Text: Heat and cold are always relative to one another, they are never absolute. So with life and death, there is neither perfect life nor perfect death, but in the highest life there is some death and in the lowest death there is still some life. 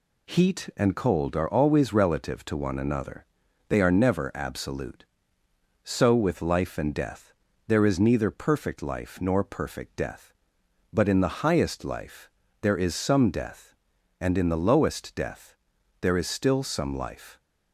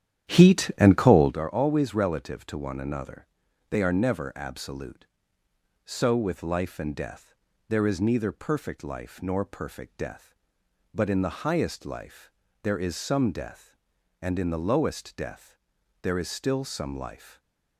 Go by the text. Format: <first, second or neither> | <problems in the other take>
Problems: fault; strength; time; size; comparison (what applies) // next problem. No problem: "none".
first | starts louder than the rest; strong; until 1.3 s; 10.5 dB // pauses between "life" and "there"; slight; at 12.2 s; 0.34 s long; slight in the first // pauses between "death" and "there"; noticeable; at 15.5 s; 0.46 s long; noticeable in the first // stays silent after the last word; slight; from 17.1 s on; 0.6 s long